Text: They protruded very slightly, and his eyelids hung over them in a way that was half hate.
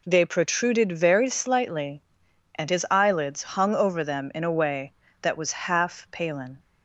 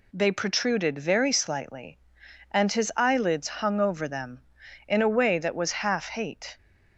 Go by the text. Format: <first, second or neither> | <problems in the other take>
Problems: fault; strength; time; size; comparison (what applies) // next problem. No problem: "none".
second | says "palin" for "hate"; at 6.1 s